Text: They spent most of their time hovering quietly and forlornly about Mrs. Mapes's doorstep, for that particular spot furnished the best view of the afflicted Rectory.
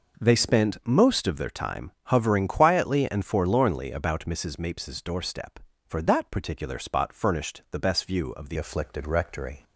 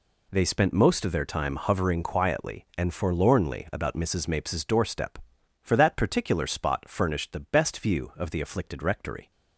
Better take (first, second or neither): second